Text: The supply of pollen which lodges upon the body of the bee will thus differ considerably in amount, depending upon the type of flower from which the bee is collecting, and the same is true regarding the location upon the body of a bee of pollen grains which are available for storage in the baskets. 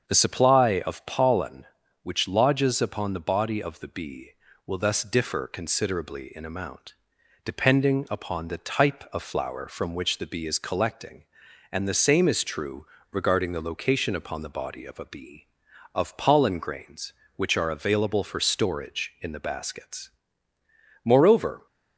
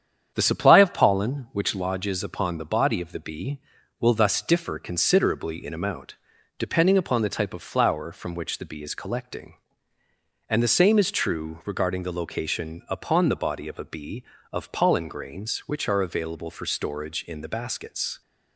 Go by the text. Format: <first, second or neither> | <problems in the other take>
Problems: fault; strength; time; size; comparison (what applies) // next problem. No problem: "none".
second | starts louder than the rest; strong; until 1.1 s; 7 dB; strong in the second // pauses between "true" and "regarding"; slight; at 12.8 s; 0.24 s long // goes on to say "Moreover"; noticeable; from 21.0 s on; 0.62 s long